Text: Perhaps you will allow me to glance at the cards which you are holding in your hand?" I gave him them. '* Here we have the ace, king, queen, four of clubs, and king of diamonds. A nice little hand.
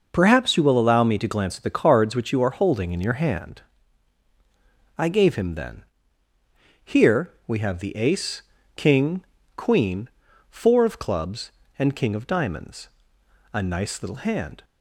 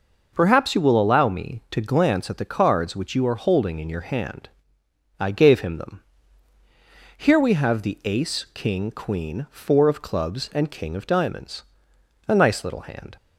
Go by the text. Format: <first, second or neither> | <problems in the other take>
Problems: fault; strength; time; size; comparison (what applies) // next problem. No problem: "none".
second | says "then" for "them"; at 5.5 s // pauses between "Here" and "we"; slight; at 7.2 s; 0.16 s long